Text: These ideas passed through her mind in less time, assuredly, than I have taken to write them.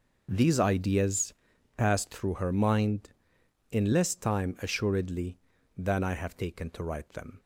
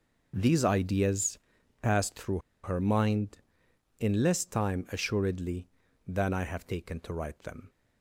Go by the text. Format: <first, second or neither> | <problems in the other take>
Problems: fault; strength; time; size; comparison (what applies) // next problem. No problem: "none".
first | pauses between "ideas" and "passed"; at 1.3 s; 0.42 s long; also in the first // pauses between "through" and "her"; slight; at 2.3 s; 0.25 s long